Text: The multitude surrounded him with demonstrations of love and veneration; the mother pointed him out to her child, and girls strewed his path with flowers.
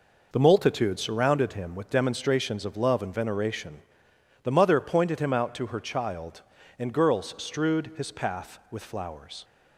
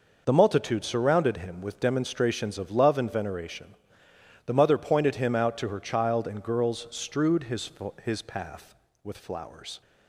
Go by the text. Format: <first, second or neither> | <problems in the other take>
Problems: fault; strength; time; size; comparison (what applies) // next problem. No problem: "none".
first | says "his" twice; at 8.0 s